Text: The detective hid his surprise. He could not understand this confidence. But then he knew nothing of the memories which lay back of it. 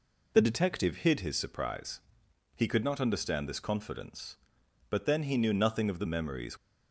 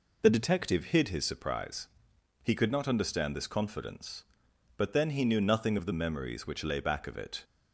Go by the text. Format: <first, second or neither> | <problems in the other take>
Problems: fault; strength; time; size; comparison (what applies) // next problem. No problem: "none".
second | stops before "which lay back of it"; at 6.5 s